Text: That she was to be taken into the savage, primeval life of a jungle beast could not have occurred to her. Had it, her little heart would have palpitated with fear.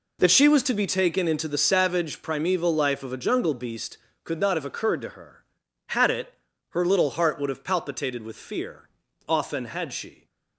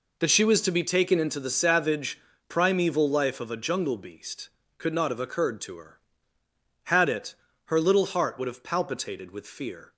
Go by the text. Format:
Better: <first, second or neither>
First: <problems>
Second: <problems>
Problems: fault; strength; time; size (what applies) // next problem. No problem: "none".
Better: second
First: goes on to say "Often had she"; noticeable; from 9.2 s on; 0.98 s long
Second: none